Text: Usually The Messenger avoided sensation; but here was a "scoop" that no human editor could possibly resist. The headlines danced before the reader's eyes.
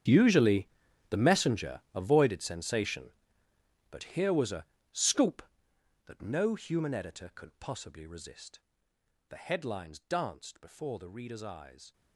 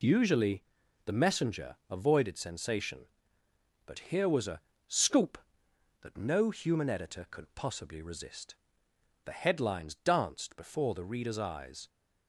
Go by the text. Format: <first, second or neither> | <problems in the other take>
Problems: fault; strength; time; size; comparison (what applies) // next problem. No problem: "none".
second | gets quieter; strong; throughout; 18.5 dB // pauses between "Usually" and "The"; at 0.6 s; 0.42 s long; also in the second // pauses between "a" and "scoop"; slight; at 4.6 s; 0.28 s long; slight in the second